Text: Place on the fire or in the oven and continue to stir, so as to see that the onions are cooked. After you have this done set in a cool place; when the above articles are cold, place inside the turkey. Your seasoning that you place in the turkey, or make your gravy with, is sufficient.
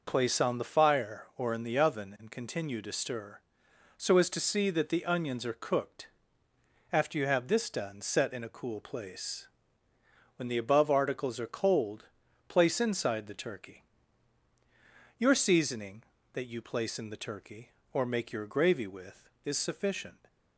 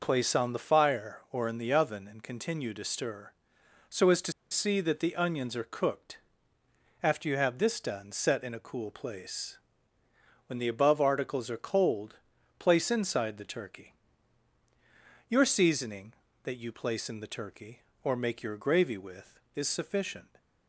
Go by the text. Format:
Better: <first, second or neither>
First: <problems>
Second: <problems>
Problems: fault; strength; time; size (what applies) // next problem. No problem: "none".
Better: first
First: none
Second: pauses between "to" and "see"; slight; at 4.3 s; 0.18 s long